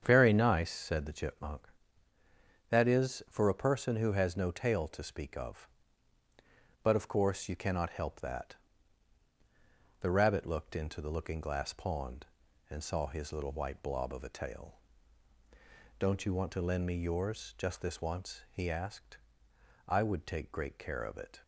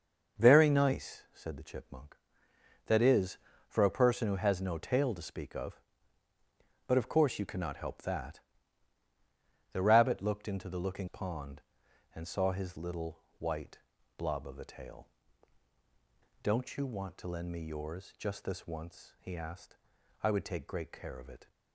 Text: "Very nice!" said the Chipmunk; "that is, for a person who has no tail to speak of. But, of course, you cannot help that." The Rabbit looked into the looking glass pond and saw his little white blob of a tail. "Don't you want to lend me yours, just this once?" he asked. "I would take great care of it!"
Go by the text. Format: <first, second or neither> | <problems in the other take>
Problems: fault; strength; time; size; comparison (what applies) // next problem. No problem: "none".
first | starts louder than the rest; until 1.4 s; 6 dB; strong in the first // skips "glass"; at 11.0 s // pauses between "little" and "white"; slight; at 13.1 s; 0.20 s long // pauses between "white" and "blob"; at 13.7 s; 0.38 s long